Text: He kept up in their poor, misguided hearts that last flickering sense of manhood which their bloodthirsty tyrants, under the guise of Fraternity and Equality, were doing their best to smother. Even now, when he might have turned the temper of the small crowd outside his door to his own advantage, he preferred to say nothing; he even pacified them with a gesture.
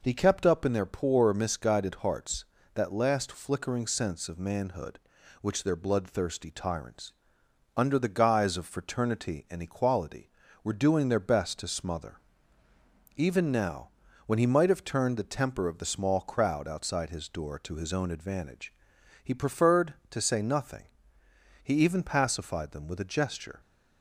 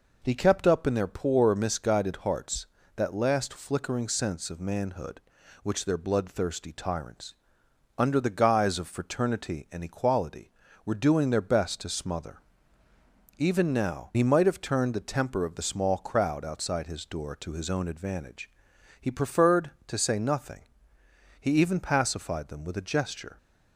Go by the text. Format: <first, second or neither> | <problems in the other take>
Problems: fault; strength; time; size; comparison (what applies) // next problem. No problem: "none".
first | skips "when"; at 14.1 s